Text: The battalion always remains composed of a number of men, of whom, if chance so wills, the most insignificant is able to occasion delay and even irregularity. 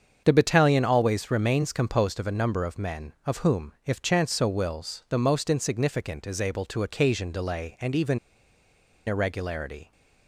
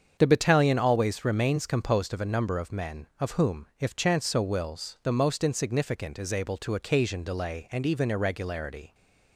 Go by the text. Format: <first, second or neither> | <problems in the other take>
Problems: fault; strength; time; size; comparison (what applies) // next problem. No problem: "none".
second | starts louder than the rest; strong; until 1.2 s; 7 dB; strong in the second // pauses between "even" and "irregularity"; noticeable; at 8.1 s; 0.90 s long